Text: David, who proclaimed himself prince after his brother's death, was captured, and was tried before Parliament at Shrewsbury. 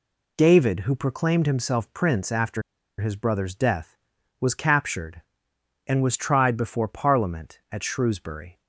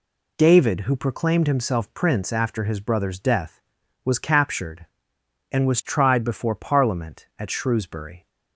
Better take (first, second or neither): second